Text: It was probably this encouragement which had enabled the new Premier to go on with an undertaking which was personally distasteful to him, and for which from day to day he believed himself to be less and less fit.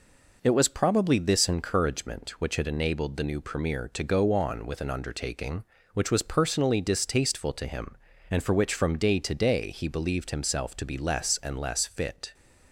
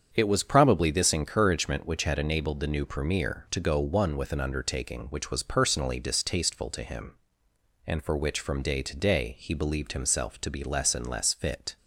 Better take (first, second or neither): first